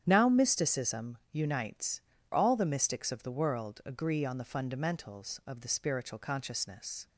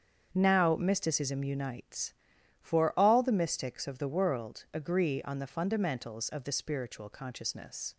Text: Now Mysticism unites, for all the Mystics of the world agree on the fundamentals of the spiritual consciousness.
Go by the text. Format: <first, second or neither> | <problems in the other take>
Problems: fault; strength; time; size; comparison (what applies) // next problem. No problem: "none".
second | starts louder than the rest; strong; until 1.0 s; 9.5 dB; strong in the second // pauses between "Mysticism" and "unites"; slight; at 1.1 s; 0.16 s long // skips "for"; at 2.1 s